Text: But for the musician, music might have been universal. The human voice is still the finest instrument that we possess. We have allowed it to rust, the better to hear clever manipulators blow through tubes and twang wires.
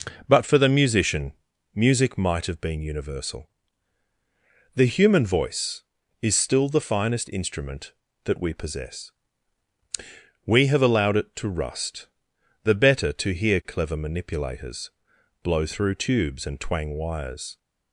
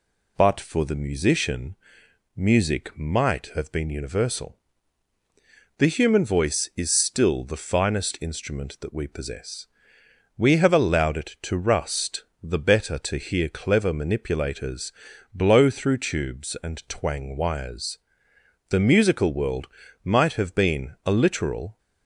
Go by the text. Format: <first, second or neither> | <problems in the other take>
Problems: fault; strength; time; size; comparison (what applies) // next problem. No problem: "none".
first | pauses between "manipulators" and "blow"; at 14.9 s; 0.42 s long; noticeable in the first // goes on to say "The musical world might have been a literal"; strong; from 18.6 s on; 3.0 s long